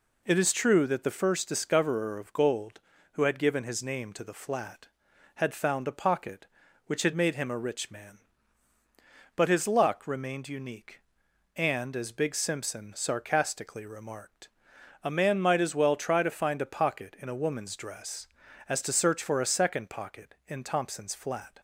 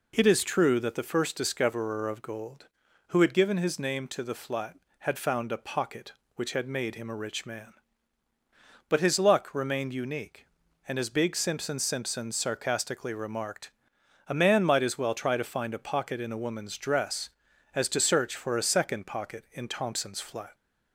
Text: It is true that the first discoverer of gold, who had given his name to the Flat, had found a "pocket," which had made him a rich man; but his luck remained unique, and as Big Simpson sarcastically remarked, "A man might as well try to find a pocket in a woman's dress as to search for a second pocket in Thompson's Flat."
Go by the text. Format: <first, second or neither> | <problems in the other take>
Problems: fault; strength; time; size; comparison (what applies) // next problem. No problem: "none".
first | says "Simpson" twice; at 11.8 s